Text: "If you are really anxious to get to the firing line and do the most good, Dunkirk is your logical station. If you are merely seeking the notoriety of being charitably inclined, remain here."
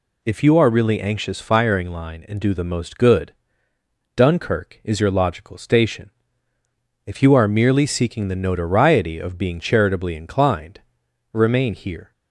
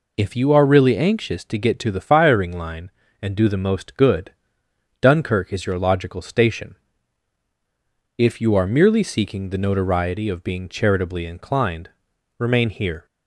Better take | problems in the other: second | skips "to get to the"; at 1.4 s

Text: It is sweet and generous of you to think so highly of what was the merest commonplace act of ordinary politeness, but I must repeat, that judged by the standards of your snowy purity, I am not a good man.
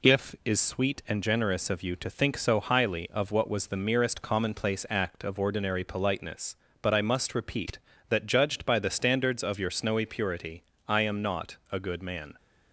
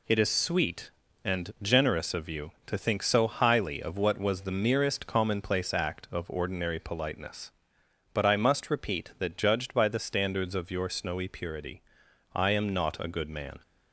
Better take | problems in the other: second | says "If" for "It"; at 0.0 s

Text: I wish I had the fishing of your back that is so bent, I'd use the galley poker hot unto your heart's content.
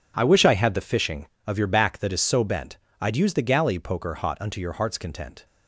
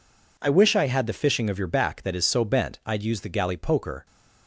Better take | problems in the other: first | stops before "hot unto your heart's content"; at 4.0 s

